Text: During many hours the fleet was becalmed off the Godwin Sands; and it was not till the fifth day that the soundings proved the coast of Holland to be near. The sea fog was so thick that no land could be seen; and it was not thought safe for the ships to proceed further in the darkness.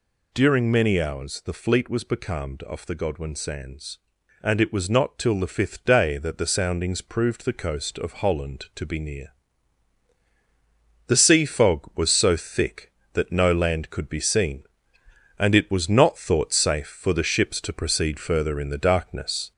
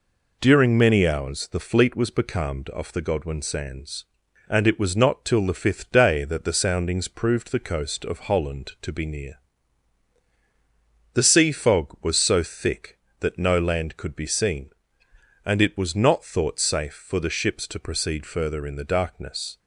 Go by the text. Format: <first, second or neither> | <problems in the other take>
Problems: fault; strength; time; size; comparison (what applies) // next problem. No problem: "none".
second | gets louder; slight; throughout; 3 dB